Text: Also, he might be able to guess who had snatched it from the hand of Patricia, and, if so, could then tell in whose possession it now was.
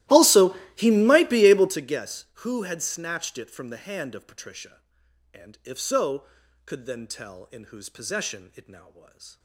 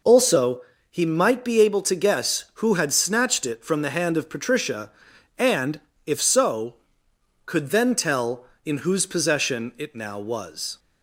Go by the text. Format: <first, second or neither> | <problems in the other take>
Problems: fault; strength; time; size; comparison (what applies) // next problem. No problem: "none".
second | starts louder than the rest; strong; until 1.8 s; 15.5 dB